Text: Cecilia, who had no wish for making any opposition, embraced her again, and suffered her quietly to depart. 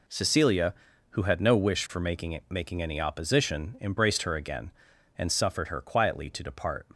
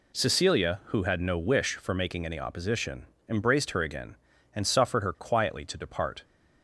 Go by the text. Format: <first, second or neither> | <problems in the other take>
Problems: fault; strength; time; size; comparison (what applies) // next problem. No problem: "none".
second | says "making" twice; at 2.4 s